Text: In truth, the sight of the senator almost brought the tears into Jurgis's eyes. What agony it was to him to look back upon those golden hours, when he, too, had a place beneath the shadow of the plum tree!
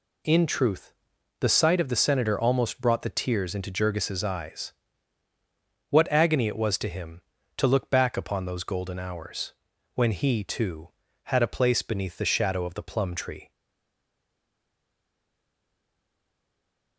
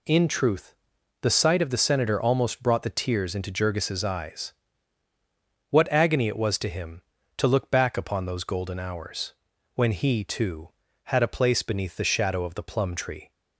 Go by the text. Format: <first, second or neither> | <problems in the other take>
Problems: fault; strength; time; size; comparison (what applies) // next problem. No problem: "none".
second | stays silent after the last word; strong; from 13.5 s on; 3.4 s long